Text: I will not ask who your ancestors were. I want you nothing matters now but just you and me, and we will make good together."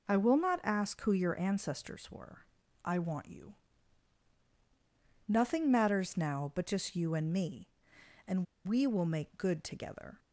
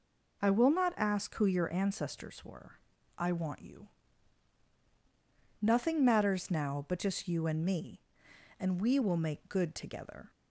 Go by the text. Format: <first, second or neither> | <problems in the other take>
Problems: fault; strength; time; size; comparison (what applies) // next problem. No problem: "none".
second | pauses between "you" and "nothing"; strong; at 3.5 s; 1.7 s long; strong in the second // pauses between "and" and "we"; slight; at 8.4 s; 0.23 s long